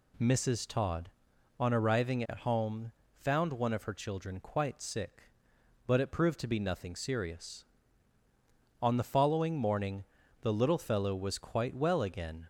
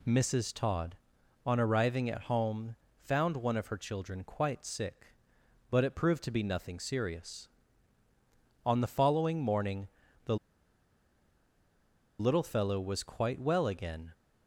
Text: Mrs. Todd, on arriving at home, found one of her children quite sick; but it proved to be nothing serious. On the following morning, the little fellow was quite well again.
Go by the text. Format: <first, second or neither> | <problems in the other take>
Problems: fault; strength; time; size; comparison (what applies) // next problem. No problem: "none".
first | pauses between "the" and "little"; strong; at 10.3 s; 1.8 s long